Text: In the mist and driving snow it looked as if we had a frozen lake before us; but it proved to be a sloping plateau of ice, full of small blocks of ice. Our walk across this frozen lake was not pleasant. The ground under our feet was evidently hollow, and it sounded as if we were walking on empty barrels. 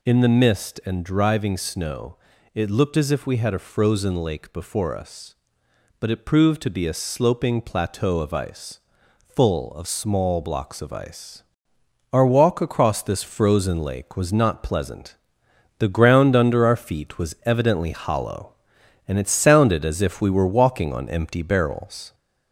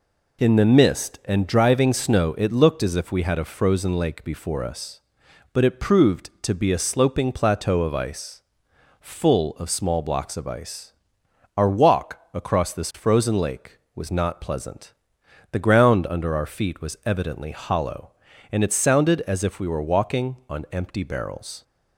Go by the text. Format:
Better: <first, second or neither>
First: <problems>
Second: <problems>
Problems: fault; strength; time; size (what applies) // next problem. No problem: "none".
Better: second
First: gets louder; slight; throughout; 2.5 dB // pauses between "snow" and "it"; at 2.1 s; 0.38 s long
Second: none